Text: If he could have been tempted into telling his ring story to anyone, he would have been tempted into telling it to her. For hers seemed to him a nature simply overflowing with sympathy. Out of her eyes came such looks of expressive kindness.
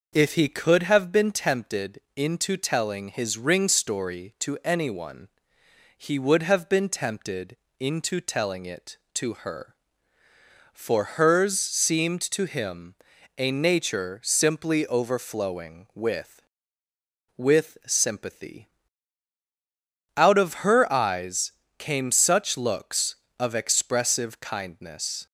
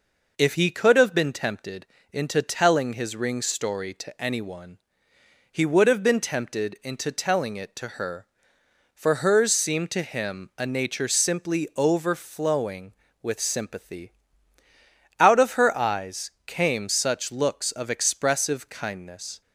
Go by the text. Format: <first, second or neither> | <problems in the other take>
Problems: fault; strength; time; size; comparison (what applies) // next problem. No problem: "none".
second | pauses between "tempted" and "into"; slight; at 1.9 s; 0.18 s long; slight in the second // pauses between "tempted" and "into"; slight; at 7.5 s; 0.24 s long // pauses between "him" and "a"; at 12.9 s; 0.44 s long // says "with" twice; at 17.3 s // pauses between "eyes" and "came"; slight; at 21.4 s; 0.30 s long; slight in the second